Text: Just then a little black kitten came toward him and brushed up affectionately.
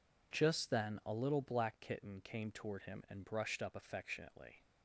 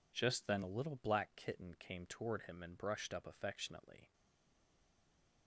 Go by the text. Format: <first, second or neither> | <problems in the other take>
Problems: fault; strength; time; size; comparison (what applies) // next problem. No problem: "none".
first | stays silent after the last word; noticeable; from 4.1 s on; 1.3 s long